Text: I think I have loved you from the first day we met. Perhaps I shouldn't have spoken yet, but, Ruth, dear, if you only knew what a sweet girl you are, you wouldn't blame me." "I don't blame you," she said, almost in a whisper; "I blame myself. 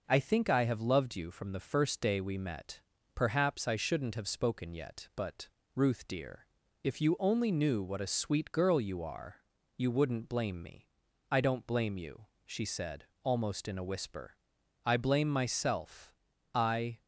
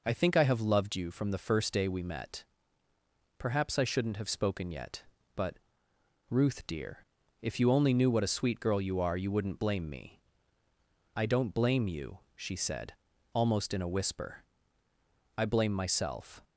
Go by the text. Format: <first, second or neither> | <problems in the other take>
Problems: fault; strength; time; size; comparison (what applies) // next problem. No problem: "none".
second | goes on to say "I"; slight; from 16.5 s on; 0.46 s long